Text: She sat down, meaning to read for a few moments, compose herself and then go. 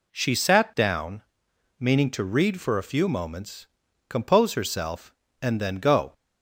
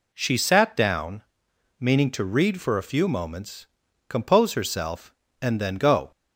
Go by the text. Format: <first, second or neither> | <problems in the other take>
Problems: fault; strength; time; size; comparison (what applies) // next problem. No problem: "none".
neither | none